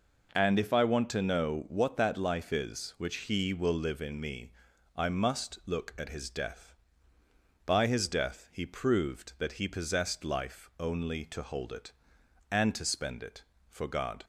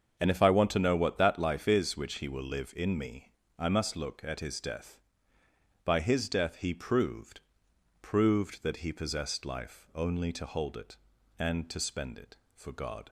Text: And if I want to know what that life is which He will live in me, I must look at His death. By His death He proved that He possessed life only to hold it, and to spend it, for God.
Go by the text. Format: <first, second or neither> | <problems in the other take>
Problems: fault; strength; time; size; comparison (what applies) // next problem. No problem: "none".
first | starts louder than the rest; until 1.1 s; 6.5 dB // says "proved" twice; at 8.0 s